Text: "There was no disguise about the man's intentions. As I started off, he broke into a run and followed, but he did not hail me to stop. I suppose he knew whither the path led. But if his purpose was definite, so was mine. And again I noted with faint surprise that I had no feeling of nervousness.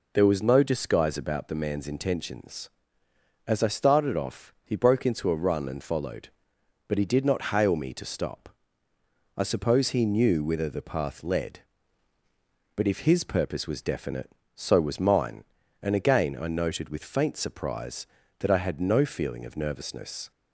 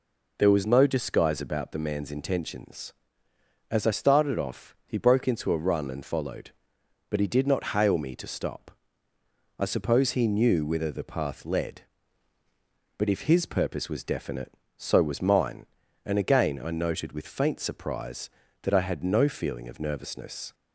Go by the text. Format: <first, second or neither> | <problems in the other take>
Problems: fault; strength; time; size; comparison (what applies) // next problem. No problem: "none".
neither | none